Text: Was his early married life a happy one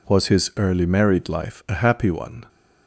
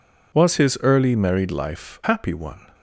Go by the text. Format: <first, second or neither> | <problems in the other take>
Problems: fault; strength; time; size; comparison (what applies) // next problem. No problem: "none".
first | skips "a"; at 2.0 s